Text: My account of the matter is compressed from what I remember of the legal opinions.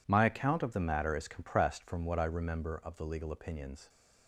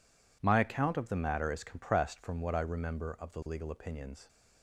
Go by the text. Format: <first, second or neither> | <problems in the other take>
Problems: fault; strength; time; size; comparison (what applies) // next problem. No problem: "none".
neither | none